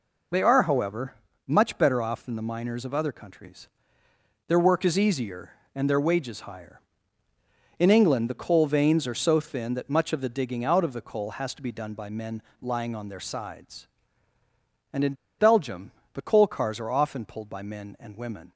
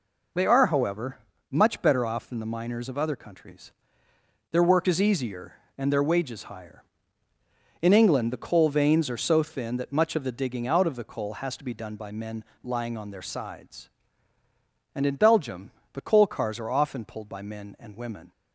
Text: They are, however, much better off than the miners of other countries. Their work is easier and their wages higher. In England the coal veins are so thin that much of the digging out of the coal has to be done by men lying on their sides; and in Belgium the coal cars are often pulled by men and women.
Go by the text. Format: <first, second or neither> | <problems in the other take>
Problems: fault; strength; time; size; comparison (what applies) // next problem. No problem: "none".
second | pauses between "men" and "lying"; slight; at 12.4 s; 0.20 s long; slight in the second // pauses between "in" and "Belgium"; slight; at 15.1 s; 0.25 s long // pauses between "Belgium" and "the"; slight; at 15.9 s; 0.20 s long; slight in the second